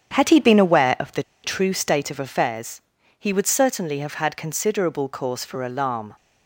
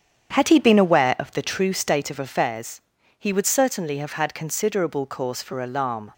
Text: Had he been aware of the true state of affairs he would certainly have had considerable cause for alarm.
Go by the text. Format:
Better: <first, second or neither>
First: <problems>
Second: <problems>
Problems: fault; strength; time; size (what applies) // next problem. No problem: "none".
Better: second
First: starts louder than the rest; strong; until 1.1 s; 8.5 dB // pauses between "the" and "true"; slight; at 1.2 s; 0.21 s long // pauses between "affairs" and "he"; at 2.7 s; 0.40 s long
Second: starts louder than the rest; strong; until 1.3 s; 8.5 dB // pauses between "affairs" and "he"; at 2.7 s; 0.40 s long